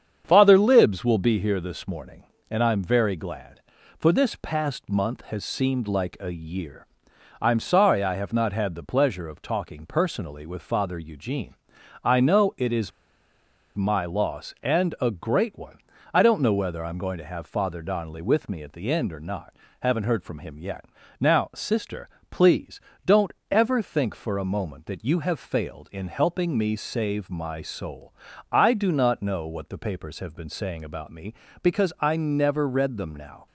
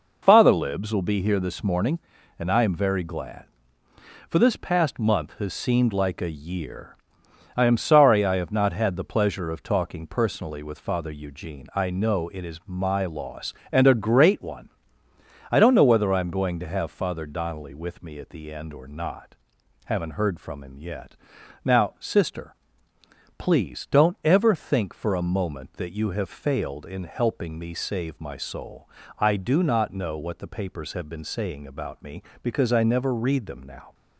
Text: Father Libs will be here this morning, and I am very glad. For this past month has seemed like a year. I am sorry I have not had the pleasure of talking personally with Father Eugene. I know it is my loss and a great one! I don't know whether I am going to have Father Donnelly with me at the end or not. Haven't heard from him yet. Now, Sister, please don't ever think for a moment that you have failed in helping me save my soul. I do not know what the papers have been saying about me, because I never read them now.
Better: second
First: starts louder than the rest; strong; until 1.2 s; 8 dB // pauses between "is" and "my"; noticeable; at 12.9 s; 0.85 s long // pauses between "please" and "don't"; slight; at 22.7 s; 0.26 s long // pauses between "don't" and "ever"; slight; at 23.2 s; 0.18 s long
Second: none

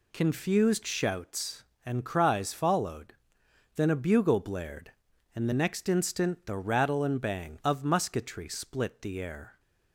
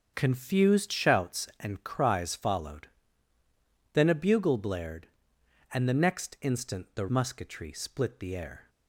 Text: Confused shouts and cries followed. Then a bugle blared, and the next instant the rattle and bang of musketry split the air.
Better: first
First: none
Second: starts louder than the rest; until 1.1 s; 7 dB // skips "rattle and bang of"; at 7.0 s

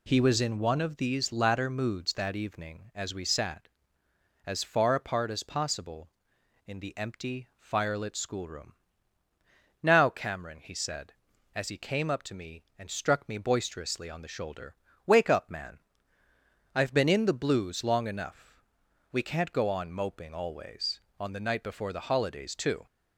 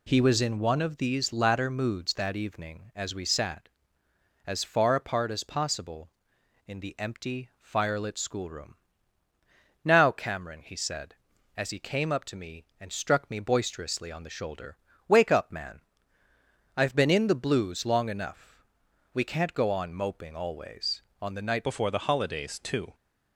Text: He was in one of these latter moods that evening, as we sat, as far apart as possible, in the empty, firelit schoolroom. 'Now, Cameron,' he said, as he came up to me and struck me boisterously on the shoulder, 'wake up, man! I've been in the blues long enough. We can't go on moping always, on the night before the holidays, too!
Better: first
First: none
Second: changes voice at "before"; from 21.6 s on; 1.3 s long

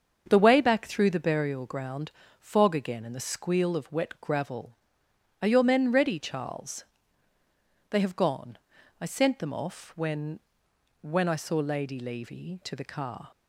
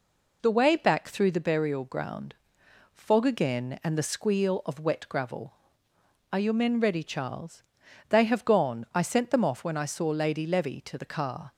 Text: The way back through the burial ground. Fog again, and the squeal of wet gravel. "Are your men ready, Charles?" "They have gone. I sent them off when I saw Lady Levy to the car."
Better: second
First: starts louder than the rest; until 1.2 s; 7 dB // says "when" twice; at 11.0 s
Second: none

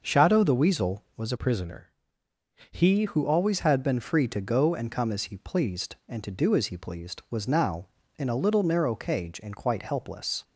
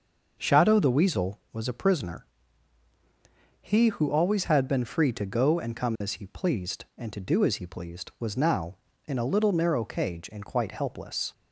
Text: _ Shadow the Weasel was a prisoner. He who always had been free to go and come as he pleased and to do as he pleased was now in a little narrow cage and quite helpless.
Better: second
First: starts louder than the rest; until 1.0 s; 6 dB // changes voice from "prisoner" to "He"; from 1.3 to 3.0 s; 1.7 s long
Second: starts louder than the rest; until 1.4 s; 6 dB

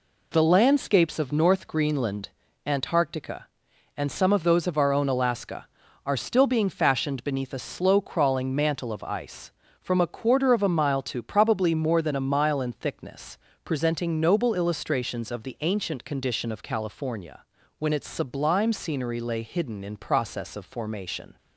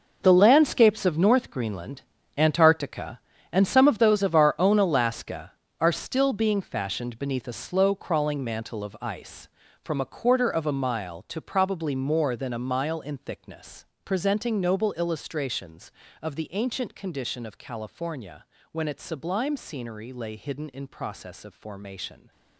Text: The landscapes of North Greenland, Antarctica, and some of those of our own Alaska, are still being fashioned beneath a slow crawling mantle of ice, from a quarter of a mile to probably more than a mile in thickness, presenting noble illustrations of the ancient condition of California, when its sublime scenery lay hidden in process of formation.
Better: first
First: none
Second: gets quieter; strong; throughout; 13 dB

